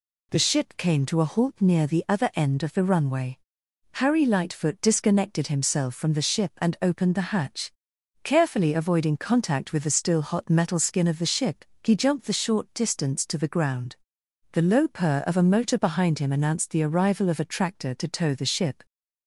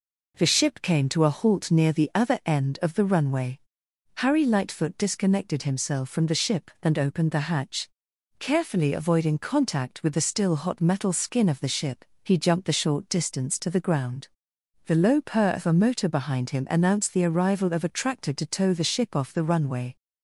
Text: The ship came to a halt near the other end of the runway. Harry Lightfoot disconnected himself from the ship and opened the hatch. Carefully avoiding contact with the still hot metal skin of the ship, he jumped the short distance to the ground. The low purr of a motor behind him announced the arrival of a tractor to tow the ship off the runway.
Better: second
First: stops before "off the runway"; at 18.8 s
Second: none

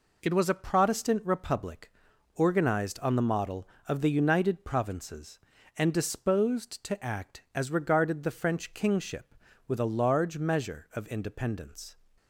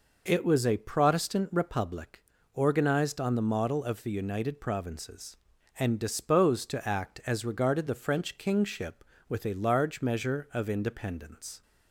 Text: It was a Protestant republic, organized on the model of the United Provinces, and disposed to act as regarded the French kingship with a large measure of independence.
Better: neither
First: none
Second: none

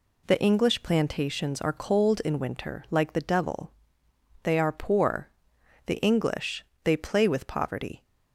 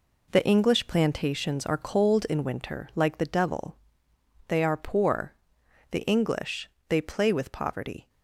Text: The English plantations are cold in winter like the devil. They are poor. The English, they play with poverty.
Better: first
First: none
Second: gets quieter; strong; throughout; 8 dB

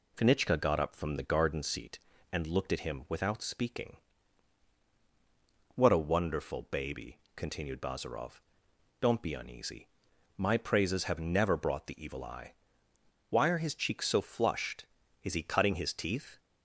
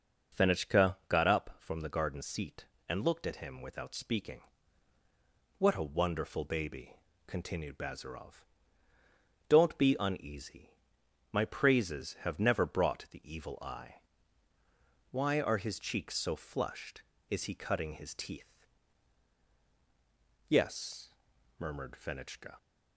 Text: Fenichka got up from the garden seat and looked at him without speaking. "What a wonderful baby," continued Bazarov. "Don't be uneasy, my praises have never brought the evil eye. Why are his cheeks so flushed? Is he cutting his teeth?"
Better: first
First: none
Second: goes on to say "Yes murmured Fenichka"; strong; from 20.4 s on; 2.0 s long

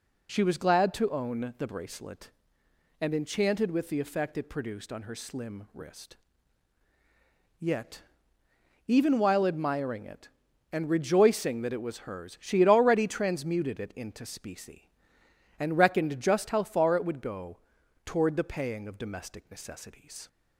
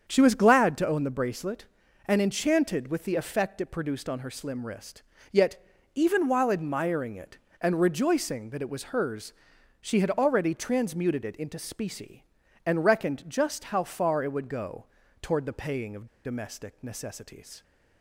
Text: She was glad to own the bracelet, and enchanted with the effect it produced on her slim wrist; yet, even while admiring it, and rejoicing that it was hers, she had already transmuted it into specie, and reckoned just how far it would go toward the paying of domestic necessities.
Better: first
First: pauses between "go" and "toward"; at 17.5 s; 0.44 s long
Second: starts louder than the rest; strong; until 1.0 s; 7.5 dB // pauses between "go" and "toward"; slight; at 14.8 s; 0.34 s long // pauses between "of" and "domestic"; slight; at 16.0 s; 0.19 s long

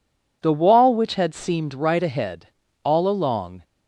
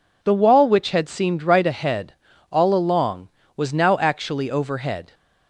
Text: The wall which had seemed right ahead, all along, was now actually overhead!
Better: second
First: stops before "was now actually overhead"; at 3.6 s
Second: none

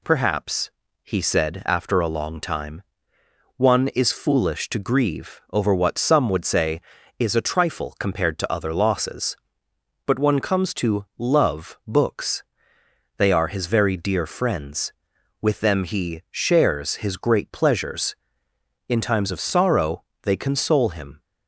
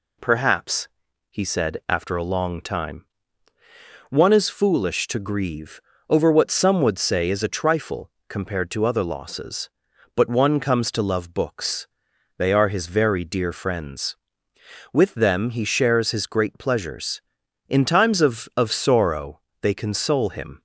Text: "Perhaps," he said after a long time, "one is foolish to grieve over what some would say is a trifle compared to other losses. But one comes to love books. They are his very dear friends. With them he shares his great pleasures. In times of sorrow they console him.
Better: first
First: pauses between "sorrow" and "they"; slight; at 20.0 s; 0.20 s long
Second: pauses between "grieve" and "over"; slight; at 5.7 s; 0.30 s long // pauses between "trifle" and "compared"; slight; at 8.0 s; 0.18 s long // says "of" twice; at 18.5 s // pauses between "sorrow" and "they"; slight; at 19.3 s; 0.22 s long

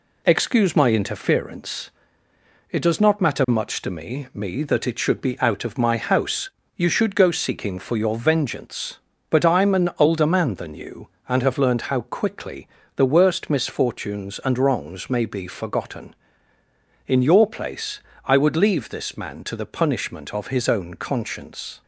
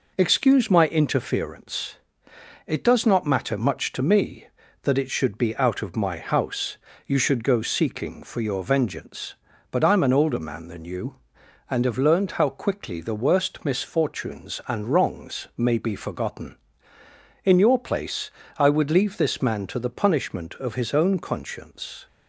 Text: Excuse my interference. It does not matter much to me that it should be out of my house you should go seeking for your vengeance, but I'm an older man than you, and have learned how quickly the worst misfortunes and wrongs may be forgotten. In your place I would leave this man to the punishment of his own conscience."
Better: second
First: says "me" twice; at 4.3 s // pauses between "house" and "you"; slight; at 6.5 s; 0.26 s long // pauses between "quickly" and "the"; slight; at 12.6 s; 0.30 s long // pauses between "place" and "I"; slight; at 18.0 s; 0.24 s long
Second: pauses between "house" and "you"; slight; at 6.7 s; 0.30 s long // pauses between "place" and "I"; slight; at 18.2 s; 0.28 s long

